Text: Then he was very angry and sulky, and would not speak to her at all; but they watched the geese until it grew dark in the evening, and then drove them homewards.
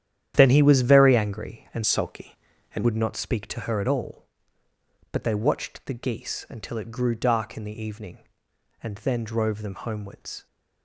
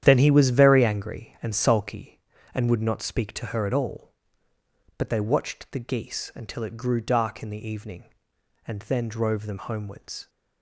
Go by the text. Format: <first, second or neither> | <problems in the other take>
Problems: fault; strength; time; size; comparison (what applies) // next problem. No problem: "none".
second | starts louder than the rest; strong; until 1.3 s; 10.5 dB; strong in the second // changes voice from "sulky" to "and"; from 1.8 to 2.8 s; 1.0 s long